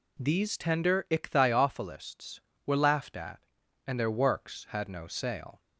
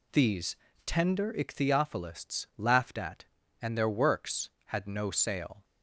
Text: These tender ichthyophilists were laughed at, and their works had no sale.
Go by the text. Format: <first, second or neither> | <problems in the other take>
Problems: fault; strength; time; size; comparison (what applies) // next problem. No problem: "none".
first | pauses between "These" and "tender"; slight; at 0.5 s; 0.30 s long // skips "were"; at 2.5 s